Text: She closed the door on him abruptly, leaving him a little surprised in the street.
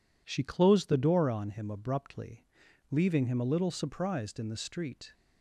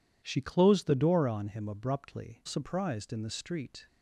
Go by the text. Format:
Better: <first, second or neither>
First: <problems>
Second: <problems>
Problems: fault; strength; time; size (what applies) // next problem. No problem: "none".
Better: first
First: none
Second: skips "leaving him a little"; at 2.4 s